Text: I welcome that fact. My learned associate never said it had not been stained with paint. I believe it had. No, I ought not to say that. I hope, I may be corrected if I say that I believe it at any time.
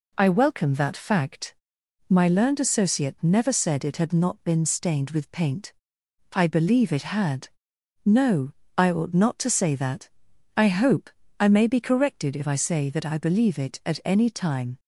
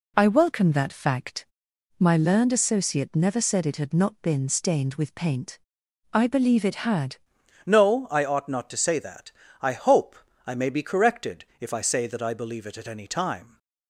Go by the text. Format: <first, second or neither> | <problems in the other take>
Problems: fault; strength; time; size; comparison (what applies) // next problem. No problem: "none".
first | changes voice at "No"; from 7.6 s on; 5.9 s long // pauses between "corrected" and "if"; slight; at 11.4 s; 0.16 s long